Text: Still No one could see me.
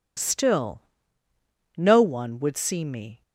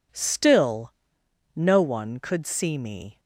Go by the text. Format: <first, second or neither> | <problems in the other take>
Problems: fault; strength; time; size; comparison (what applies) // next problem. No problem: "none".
second | pauses between "Still" and "No"; noticeable; at 0.8 s; 0.94 s long; noticeable in the second // says "would" for "could"; at 2.3 s